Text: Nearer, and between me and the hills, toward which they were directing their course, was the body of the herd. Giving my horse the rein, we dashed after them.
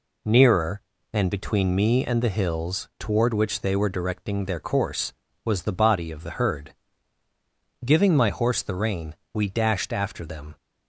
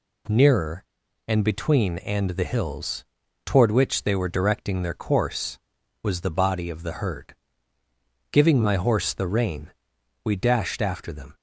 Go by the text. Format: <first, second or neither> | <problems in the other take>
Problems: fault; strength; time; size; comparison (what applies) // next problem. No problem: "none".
first | skips "me"; at 1.9 s